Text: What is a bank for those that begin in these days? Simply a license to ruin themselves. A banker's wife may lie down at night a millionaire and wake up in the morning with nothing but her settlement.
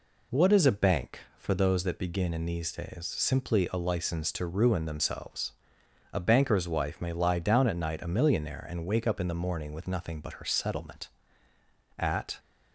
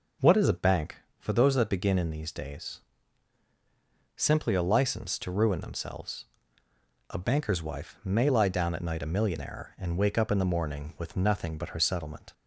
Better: second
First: goes on to say "At"; slight; from 11.9 s on; 0.40 s long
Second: none

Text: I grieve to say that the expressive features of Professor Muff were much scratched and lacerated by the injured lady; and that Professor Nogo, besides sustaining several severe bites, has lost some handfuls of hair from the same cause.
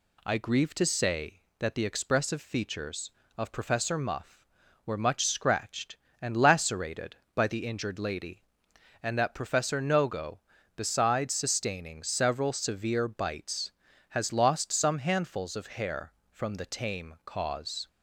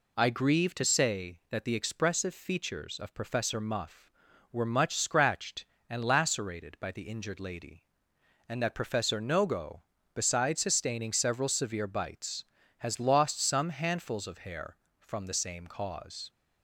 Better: second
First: says "tame" for "same"; at 16.6 s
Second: none

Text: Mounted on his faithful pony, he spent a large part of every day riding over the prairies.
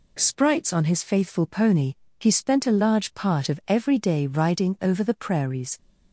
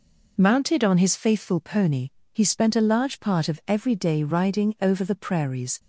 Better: second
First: says "Sprites" for "Mounted"; at 0.1 s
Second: none

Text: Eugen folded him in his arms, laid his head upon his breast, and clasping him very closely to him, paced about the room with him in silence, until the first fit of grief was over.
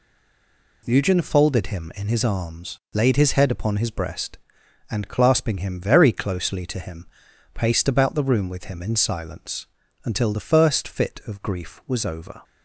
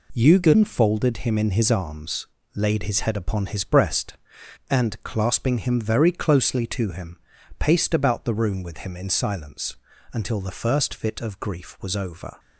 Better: second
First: stays silent before the first word; slight; until 0.8 s; 0.8 s long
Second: none

